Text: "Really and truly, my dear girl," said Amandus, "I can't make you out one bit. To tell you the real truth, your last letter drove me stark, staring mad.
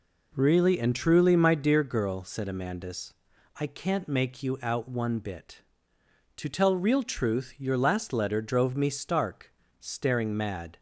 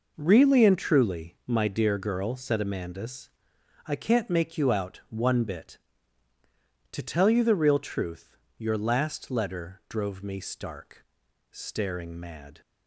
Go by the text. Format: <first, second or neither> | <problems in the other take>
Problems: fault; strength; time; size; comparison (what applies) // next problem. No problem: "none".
second | skips "you the"; at 6.7 s